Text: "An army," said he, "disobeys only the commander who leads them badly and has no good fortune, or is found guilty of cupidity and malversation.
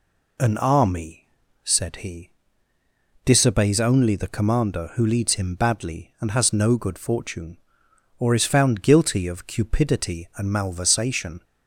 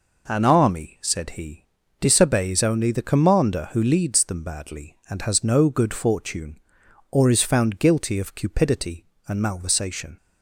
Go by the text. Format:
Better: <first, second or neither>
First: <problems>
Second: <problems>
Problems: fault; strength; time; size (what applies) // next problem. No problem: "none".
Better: second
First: says "him" for "them"; at 5.3 s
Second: none